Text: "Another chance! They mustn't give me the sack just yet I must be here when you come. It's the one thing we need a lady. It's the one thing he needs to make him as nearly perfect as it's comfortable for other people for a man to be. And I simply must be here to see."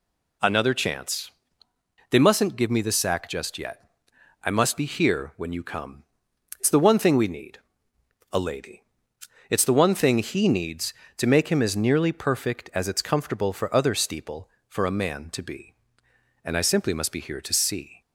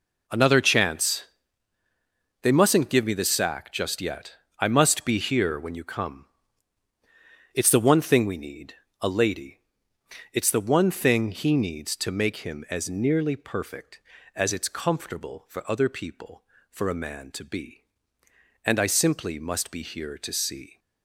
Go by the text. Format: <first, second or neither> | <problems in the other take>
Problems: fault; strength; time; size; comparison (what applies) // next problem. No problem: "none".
second | pauses between "yet" and "I"; noticeable; at 3.8 s; 0.56 s long; slight in the second // pauses between "need" and "a"; noticeable; at 7.5 s; 0.74 s long; slight in the second // says "steeple" for "people"; at 13.9 s